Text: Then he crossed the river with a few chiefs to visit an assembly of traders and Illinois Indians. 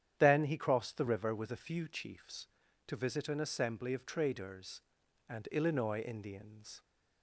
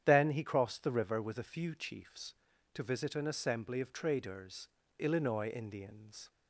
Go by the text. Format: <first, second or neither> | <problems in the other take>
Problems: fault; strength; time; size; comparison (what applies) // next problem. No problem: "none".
first | starts louder than the rest; strong; until 1.0 s; 9 dB; strong in the first // skips "and"; at 4.8 s